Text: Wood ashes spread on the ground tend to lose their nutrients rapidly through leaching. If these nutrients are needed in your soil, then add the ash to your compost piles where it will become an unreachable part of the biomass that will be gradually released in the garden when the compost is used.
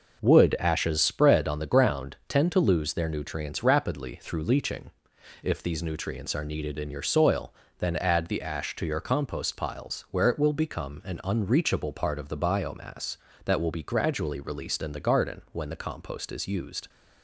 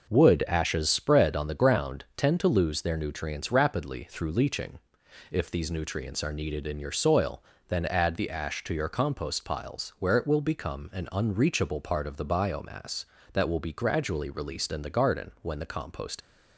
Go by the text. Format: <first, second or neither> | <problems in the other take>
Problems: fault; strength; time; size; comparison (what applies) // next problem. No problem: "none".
first | starts louder than the rest; noticeable; until 1.1 s; 6 dB; noticeable in the first // stops before "is used"; at 16.2 s